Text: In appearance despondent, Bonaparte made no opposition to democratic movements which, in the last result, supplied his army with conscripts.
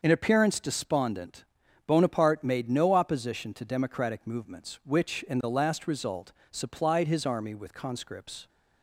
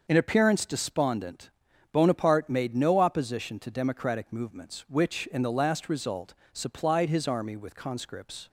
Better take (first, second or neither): neither